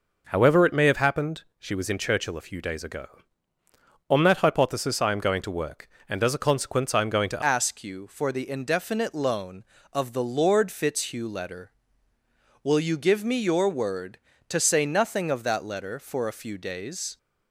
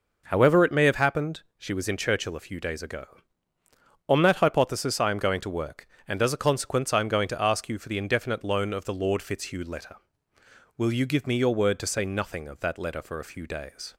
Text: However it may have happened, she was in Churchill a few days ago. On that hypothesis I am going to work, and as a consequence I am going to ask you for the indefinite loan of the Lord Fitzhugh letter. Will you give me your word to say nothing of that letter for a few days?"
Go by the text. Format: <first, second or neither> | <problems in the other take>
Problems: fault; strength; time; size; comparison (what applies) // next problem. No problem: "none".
second | changes voice at "ask"; from 7.4 s on; 9.7 s long